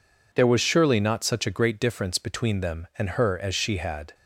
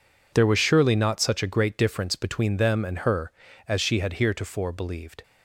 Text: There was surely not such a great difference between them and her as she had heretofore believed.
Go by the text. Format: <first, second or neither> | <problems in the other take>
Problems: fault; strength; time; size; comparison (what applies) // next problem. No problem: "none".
second | stops before "heretofore believed"; at 4.1 s